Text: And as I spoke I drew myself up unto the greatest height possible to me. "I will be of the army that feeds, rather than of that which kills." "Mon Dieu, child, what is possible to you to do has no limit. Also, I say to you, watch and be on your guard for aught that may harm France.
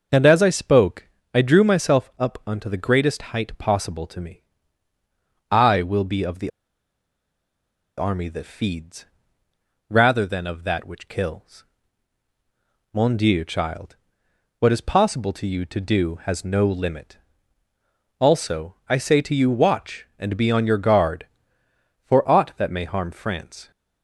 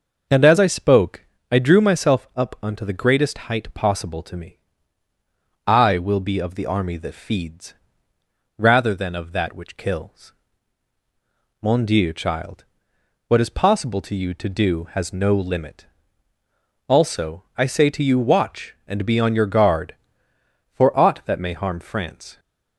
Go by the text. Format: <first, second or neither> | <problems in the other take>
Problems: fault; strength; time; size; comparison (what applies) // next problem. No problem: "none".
second | pauses between "spoke" and "I"; slight; at 1.0 s; 0.24 s long; slight in the second // pauses between "the" and "army"; strong; at 6.4 s; 1.4 s long